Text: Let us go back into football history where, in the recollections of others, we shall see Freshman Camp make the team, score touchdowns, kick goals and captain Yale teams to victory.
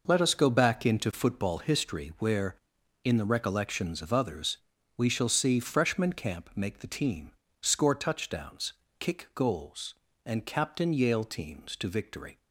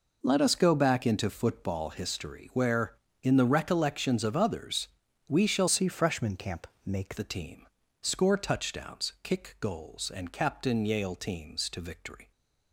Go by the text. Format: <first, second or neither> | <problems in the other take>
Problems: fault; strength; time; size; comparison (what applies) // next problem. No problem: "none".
first | changes voice from "see" to "make"; from 5.6 to 7.1 s; 1.5 s long // pauses between "Camp" and "make"; slight; at 6.6 s; 0.20 s long